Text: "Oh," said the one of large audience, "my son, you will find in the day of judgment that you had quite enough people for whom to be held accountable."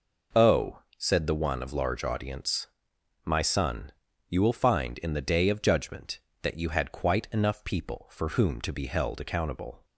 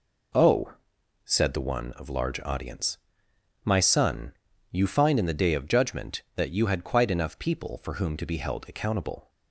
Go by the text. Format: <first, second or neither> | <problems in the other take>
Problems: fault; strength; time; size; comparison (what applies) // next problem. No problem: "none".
first | skips "will"; at 4.8 s